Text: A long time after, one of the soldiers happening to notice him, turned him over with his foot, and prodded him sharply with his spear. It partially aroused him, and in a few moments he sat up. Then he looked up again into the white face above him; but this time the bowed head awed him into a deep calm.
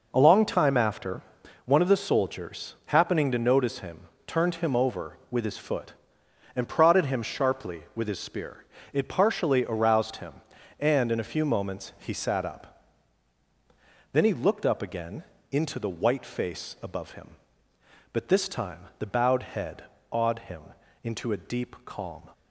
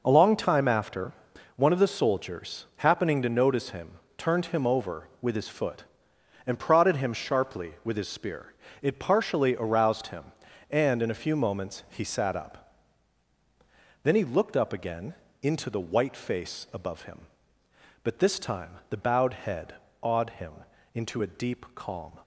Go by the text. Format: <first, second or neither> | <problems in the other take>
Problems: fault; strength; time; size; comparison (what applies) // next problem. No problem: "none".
neither | pauses between "again" and "into"; slight; the same in both // pauses between "head" and "awed"; slight; the same in both // pauses between "him" and "into"; the same in both